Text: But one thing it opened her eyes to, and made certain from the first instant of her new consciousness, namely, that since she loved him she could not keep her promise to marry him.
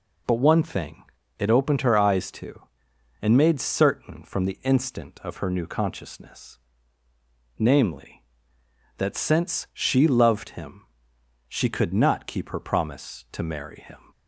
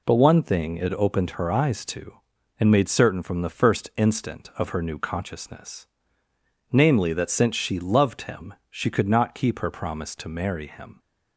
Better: second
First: pauses between "thing" and "it"; slight; at 1.0 s; 0.36 s long // skips "first"; at 4.6 s // pauses between "him" and "she"; noticeable; at 10.8 s; 0.66 s long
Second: pauses between "him" and "she"; slight; at 8.5 s; 0.16 s long

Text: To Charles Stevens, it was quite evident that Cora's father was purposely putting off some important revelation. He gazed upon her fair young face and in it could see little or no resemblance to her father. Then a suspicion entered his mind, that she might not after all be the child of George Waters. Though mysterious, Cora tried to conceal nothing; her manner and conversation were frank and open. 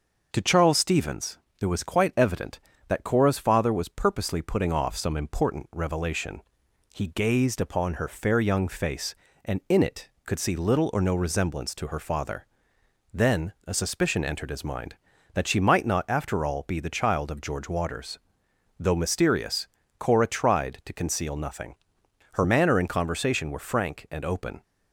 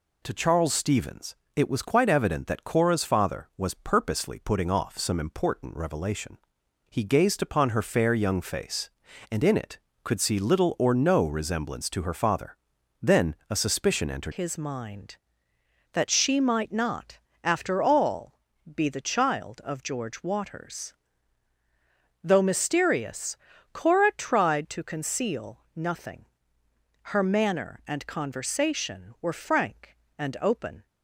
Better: first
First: none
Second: changes voice at "his"; from 14.3 s on; 16.5 s long // pauses between "not" and "after"; slight; at 17.1 s; 0.24 s long // pauses between "all" and "be"; slight; at 18.3 s; 0.36 s long // pauses between "conceal" and "nothing"; slight; at 25.6 s; 0.16 s long

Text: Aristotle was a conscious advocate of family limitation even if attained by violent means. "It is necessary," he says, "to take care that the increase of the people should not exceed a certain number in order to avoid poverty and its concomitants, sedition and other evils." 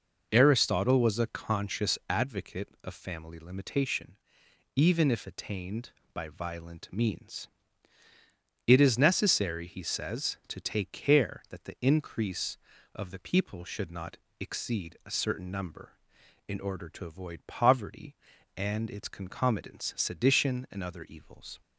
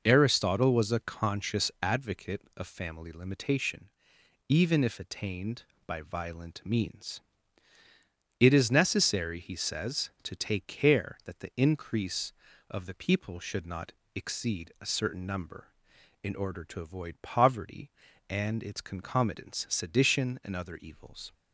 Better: neither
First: pauses between "limitation" and "even"; noticeable; at 4.1 s; 0.60 s long // pauses between "not" and "exceed"; slight; at 14.1 s; 0.22 s long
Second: pauses between "limitation" and "even"; noticeable; at 3.8 s; 0.60 s long // pauses between "not" and "exceed"; slight; at 13.9 s; 0.22 s long

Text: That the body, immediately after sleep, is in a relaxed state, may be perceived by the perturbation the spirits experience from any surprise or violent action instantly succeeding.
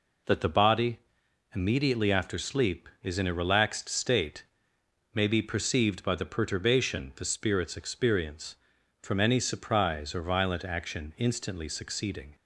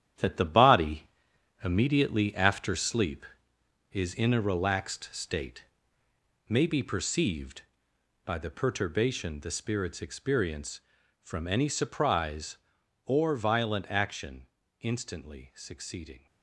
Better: first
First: none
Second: gets quieter; strong; throughout; 8.5 dB // pauses between "action" and "instantly"; slight; at 14.4 s; 0.34 s long

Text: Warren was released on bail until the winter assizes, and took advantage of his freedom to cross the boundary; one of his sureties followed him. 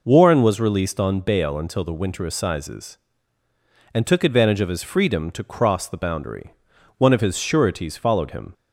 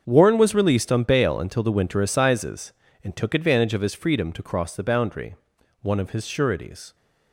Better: first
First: none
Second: starts louder than the rest; until 1.0 s; 7 dB // stops before "followed him"; at 6.9 s

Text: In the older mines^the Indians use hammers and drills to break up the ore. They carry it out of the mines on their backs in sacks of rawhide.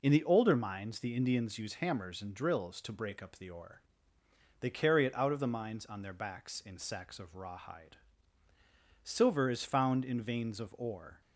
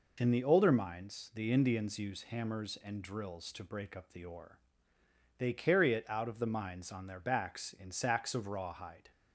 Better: second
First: goes on to say "Silver is found in veins of ore"; strong; from 9.0 s on; 2.1 s long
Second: none

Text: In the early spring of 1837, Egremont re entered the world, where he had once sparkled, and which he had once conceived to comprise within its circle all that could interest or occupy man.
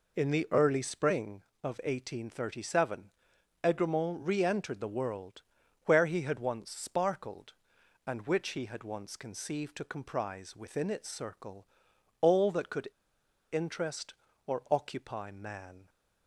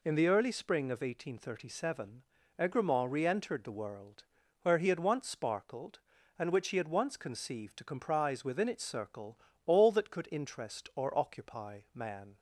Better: second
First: pauses between "circle" and "all"; noticeable; at 11.6 s; 0.54 s long // pauses between "could" and "interest"; noticeable; at 12.8 s; 0.65 s long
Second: pauses between "circle" and "all"; slight; at 9.3 s; 0.28 s long

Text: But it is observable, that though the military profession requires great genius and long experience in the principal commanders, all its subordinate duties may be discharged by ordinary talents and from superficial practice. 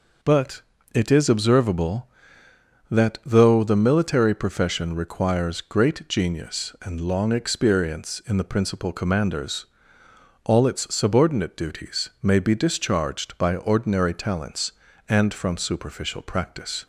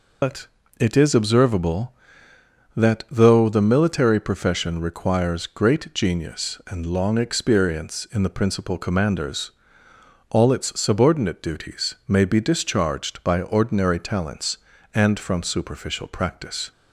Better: first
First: pauses between "But" and "it"; slight; at 0.6 s; 0.32 s long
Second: loses the start of "But"; at 0.2 s; 130 ms // pauses between "But" and "it"; slight; at 0.4 s; 0.32 s long

